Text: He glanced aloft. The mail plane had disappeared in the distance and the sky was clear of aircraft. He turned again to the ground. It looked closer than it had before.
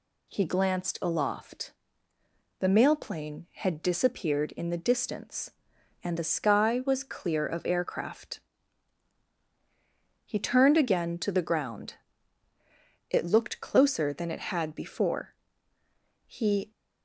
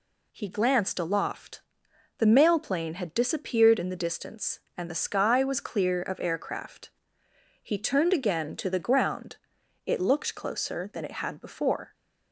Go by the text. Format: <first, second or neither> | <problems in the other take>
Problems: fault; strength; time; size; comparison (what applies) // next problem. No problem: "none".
second | goes on to say "He"; slight; from 16.2 s on; 0.44 s long